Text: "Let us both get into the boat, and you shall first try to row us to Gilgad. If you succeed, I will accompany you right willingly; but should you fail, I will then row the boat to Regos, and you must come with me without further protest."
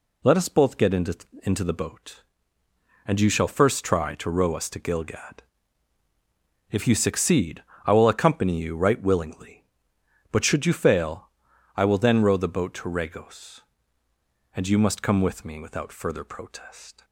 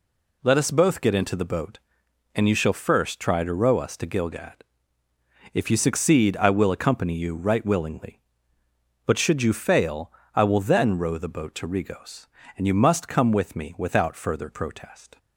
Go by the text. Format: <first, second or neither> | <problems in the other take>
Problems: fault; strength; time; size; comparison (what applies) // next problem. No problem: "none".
second | says "into" twice; at 1.4 s